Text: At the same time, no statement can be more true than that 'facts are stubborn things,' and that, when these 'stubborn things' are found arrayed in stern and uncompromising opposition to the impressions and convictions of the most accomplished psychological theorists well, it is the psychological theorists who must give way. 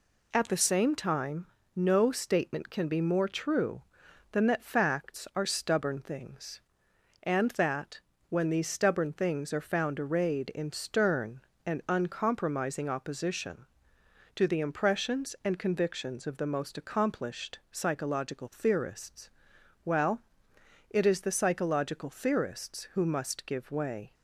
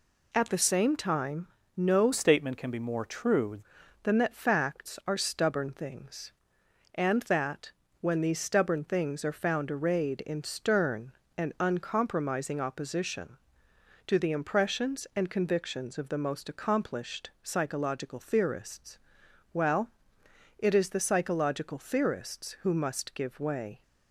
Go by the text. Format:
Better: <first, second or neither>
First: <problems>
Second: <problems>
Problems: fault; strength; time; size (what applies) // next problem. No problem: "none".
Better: first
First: pauses between "theorists" and "well"; noticeable; at 19.2 s; 0.54 s long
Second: changes voice from "statement" to "true"; from 2.1 to 3.5 s; 1.4 s long // pauses between "theorists" and "well"; noticeable; at 18.9 s; 0.54 s long